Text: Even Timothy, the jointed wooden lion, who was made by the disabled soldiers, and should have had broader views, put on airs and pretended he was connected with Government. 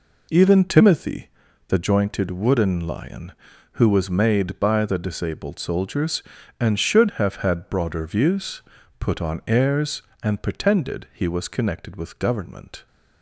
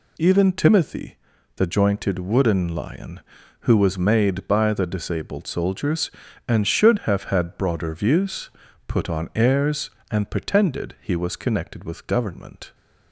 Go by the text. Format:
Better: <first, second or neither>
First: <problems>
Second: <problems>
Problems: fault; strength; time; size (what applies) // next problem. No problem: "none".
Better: second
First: starts louder than the rest; until 1.9 s; 3.5 dB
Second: none